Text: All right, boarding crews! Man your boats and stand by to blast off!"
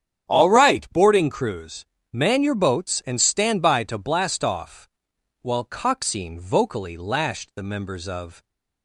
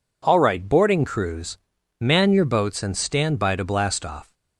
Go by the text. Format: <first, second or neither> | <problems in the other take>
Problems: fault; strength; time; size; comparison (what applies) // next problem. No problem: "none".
second | starts louder than the rest; strong; until 1.3 s; 9 dB // goes on to say "While Coxine vocally lashed the members of"; strong; from 5.4 s on; 3.0 s long